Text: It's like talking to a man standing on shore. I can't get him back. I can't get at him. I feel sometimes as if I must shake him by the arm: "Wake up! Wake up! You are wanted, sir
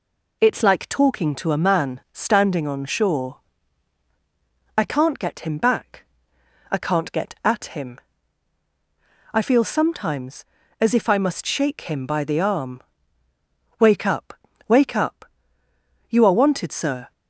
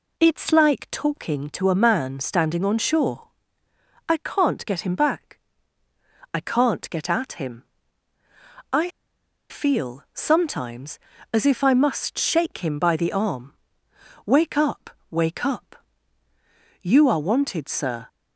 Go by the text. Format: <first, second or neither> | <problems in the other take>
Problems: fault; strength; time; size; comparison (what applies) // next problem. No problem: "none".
first | pauses between "I" and "feel"; noticeable; at 8.8 s; 0.61 s long